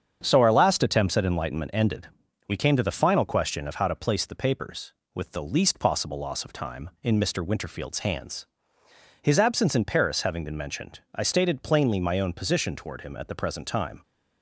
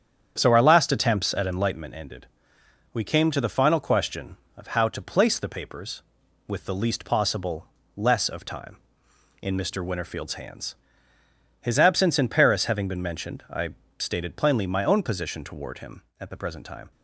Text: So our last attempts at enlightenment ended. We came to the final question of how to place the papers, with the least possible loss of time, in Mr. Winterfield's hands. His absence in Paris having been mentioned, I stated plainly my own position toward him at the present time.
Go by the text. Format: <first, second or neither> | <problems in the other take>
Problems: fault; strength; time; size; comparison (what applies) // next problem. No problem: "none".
first | starts louder than the rest; strong; until 1.3 s; 8.5 dB; strong in the first // says "less" for "loss"; at 7.9 s // pauses between "I" and "stated"; slight; at 13.6 s; 0.30 s long